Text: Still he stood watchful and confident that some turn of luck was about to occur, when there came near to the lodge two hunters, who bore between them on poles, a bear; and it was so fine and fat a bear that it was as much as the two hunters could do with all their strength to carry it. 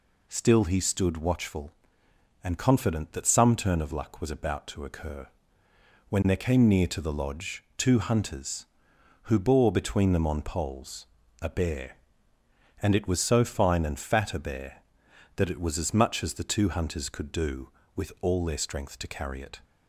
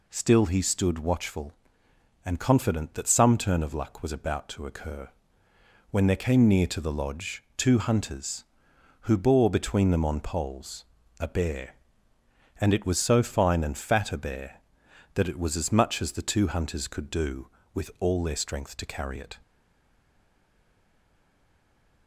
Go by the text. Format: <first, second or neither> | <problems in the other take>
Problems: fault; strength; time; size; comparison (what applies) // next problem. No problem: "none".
first | stays silent after the last word; strong; from 19.4 s on; 2.6 s long